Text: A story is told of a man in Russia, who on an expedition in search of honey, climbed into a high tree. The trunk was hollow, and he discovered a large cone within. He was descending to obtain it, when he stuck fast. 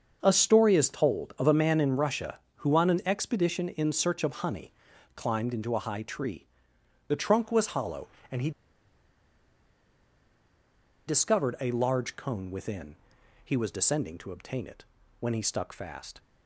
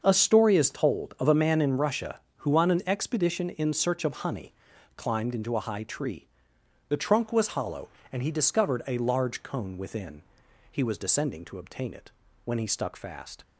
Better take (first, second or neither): second